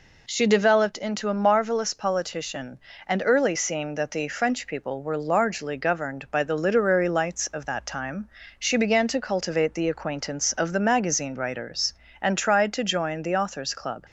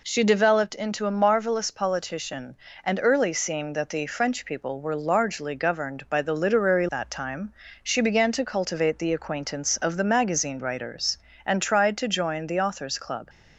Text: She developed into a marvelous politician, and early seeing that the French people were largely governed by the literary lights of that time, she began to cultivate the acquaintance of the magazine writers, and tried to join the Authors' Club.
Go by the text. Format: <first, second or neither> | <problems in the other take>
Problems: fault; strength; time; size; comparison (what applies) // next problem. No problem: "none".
first | skips "lights of"; at 6.8 s